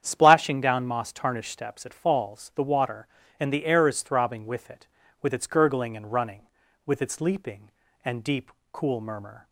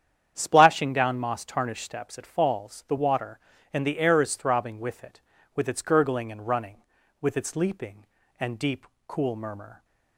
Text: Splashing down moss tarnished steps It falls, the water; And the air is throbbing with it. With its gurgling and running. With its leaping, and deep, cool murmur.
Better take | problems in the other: neither | starts louder than the rest; strong; the same in both

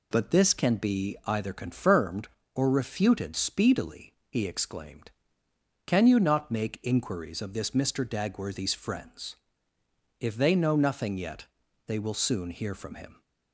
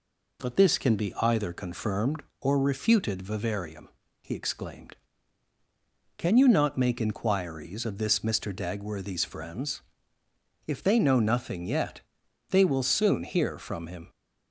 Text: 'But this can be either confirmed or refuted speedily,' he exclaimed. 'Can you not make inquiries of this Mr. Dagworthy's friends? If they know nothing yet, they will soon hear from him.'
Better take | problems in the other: first | says "vivarium" for "speedily"; at 3.2 s

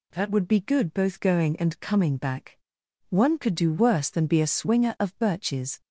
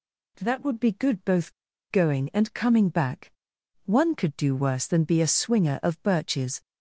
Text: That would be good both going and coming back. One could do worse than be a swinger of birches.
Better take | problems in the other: first | pauses between "both" and "going"; at 1.5 s; 0.37 s long

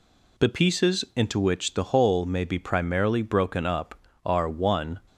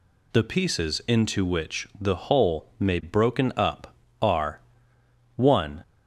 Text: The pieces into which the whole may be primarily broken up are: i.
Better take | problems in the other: first | skips "be primarily"; at 3.0 s

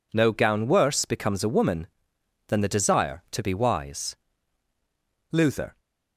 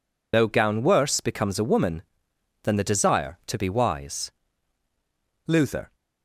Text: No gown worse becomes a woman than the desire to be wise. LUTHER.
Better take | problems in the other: first | loses the start of "No"; at 0.3 s; 75 ms

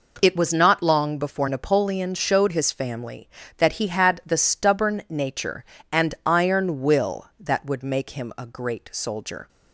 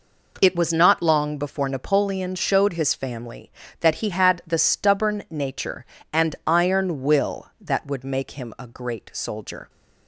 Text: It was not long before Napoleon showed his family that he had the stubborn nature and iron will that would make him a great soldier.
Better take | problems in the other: neither | none

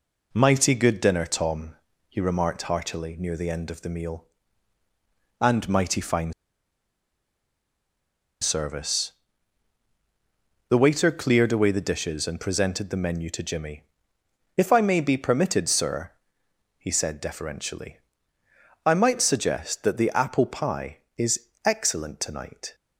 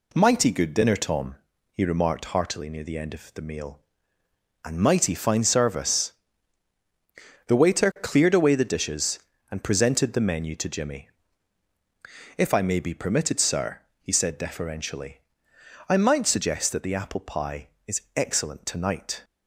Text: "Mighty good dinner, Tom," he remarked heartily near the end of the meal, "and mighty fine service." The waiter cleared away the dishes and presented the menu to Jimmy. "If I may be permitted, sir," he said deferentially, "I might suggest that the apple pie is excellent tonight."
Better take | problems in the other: second | pauses between "fine" and "service"; strong; at 6.3 s; 2.0 s long // pauses between "is" and "excellent"; slight; at 21.4 s; 0.18 s long; slight in the second

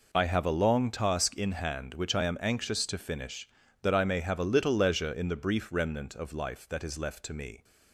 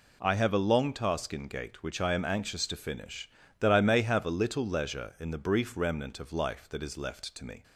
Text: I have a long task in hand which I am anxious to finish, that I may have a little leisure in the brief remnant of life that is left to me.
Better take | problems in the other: first | says "gate" for "hand"; at 1.4 s

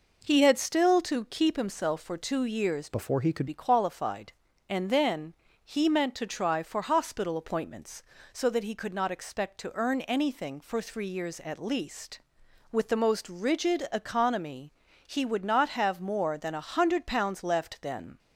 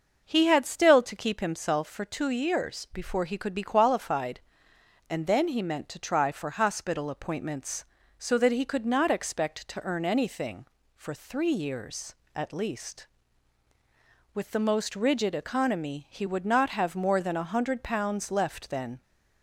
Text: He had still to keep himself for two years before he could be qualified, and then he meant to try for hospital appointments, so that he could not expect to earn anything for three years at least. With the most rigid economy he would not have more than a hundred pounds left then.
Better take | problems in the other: second | changes voice from "before" to "could"; from 2.8 to 3.4 s; 0.6 s long // pauses between "then" and "he"; slight; at 5.3 s; 0.30 s long // pauses between "economy" and "he"; slight; at 14.7 s; 0.34 s long

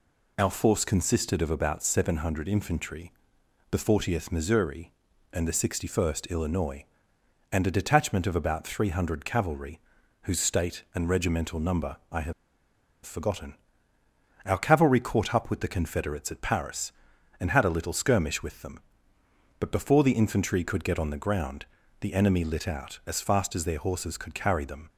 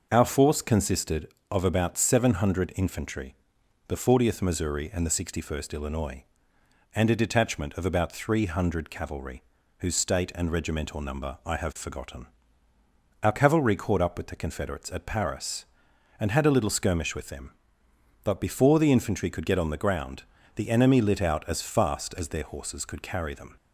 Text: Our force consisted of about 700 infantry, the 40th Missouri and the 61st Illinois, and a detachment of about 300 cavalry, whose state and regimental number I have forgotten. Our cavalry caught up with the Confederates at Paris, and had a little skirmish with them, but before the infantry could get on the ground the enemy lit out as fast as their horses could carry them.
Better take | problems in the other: second | pauses between "number" and "I"; slight; at 11.9 s; 0.16 s long // pauses between "have" and "forgotten"; noticeable; at 12.3 s; 0.71 s long // pauses between "ground" and "the"; slight; at 21.6 s; 0.34 s long; slight in the second

